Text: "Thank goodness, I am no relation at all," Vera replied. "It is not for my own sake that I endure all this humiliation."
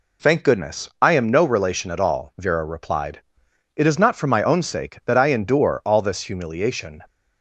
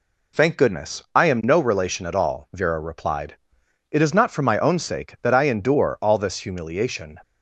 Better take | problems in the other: neither | none

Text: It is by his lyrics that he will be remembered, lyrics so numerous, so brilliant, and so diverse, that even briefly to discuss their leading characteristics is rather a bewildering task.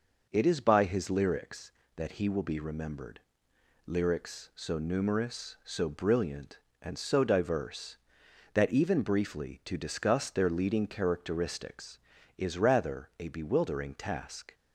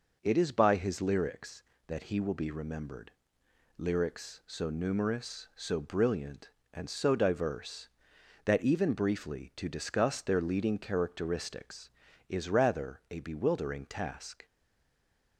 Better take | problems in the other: first | stays silent after the last word; slight; from 14.4 s on; 0.9 s long

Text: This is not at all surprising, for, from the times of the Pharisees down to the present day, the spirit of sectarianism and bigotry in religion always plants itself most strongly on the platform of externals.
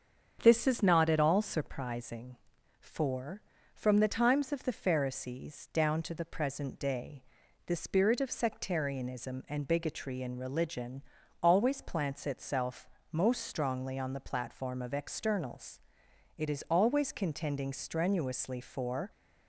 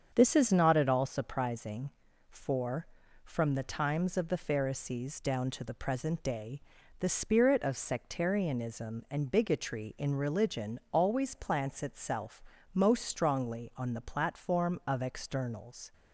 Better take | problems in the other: second | starts louder than the rest; strong; until 1.4 s; 7 dB; strong in the second // pauses between "religion" and "always"; at 11.0 s; 0.40 s long // pauses between "itself" and "most"; slight; at 12.8 s; 0.24 s long; slight in the second // goes on to say "It is always contending strenuously for"; strong; from 16.3 s on; 2.7 s long

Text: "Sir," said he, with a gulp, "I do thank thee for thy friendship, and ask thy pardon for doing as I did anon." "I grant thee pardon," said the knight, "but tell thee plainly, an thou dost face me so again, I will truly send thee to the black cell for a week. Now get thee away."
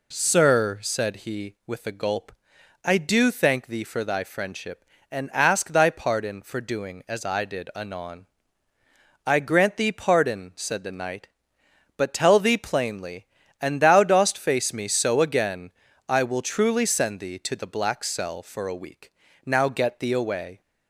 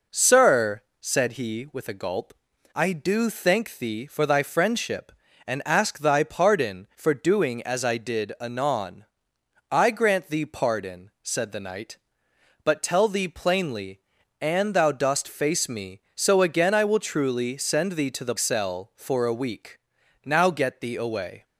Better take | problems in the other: first | skips "black"; at 18.3 s

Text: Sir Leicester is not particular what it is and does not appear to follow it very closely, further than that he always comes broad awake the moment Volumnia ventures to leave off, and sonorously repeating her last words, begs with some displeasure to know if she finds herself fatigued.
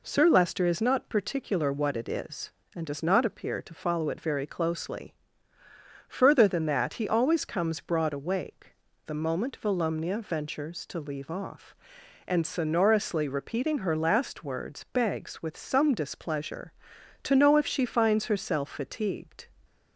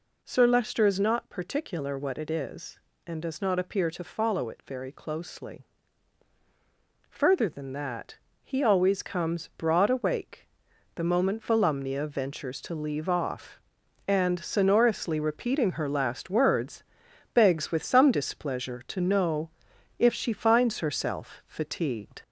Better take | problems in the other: first | gets louder; slight; throughout; 3 dB // pauses between "that" and "he"; slight; at 8.1 s; 0.28 s long // pauses between "awake" and "the"; noticeable; at 10.4 s; 0.50 s long; slight in the first // pauses between "know" and "if"; noticeable; at 19.4 s; 0.50 s long

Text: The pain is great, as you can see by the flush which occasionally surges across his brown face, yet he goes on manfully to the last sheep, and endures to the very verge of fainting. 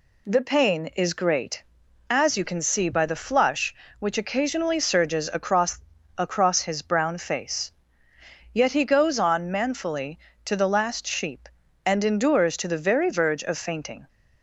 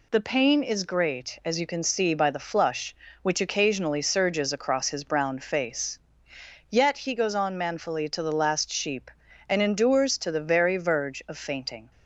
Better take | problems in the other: second | says "across" twice; at 6.1 s

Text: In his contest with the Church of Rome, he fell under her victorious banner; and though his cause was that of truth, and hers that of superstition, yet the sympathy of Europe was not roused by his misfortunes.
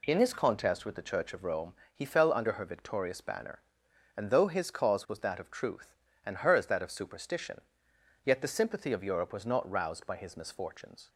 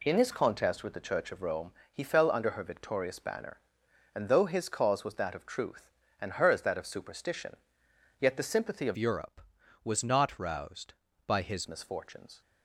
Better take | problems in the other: first | changes voice from "Europe" to "his"; from 8.9 to 11.6 s; 2.7 s long

